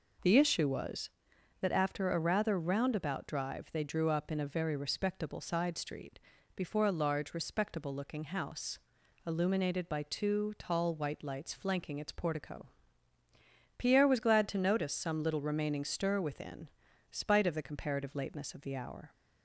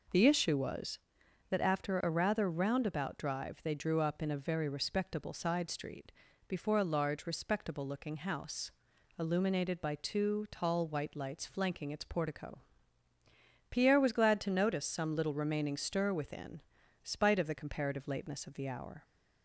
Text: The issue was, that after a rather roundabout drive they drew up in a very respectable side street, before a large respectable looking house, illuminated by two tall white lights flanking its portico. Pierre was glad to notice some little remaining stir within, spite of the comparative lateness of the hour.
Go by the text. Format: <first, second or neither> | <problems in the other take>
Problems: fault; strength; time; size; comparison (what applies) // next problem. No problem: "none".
neither | none